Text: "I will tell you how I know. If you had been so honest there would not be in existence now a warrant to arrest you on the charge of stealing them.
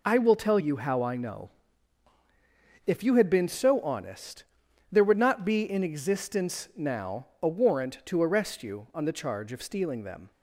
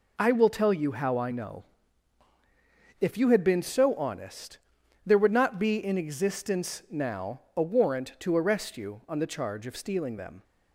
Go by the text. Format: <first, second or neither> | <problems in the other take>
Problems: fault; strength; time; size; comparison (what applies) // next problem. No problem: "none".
neither | pauses between "honest" and "there"; noticeable; the same in both